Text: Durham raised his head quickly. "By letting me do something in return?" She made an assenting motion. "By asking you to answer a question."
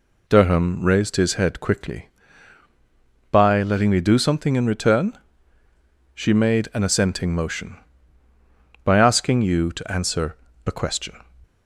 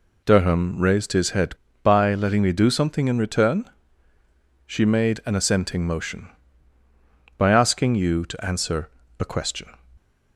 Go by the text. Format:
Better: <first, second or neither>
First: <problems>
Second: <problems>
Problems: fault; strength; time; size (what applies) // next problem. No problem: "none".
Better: first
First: pauses between "answer" and "a"; slight; at 10.3 s; 0.30 s long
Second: skips "quickly"; at 1.6 s // pauses between "answer" and "a"; slight; at 8.8 s; 0.30 s long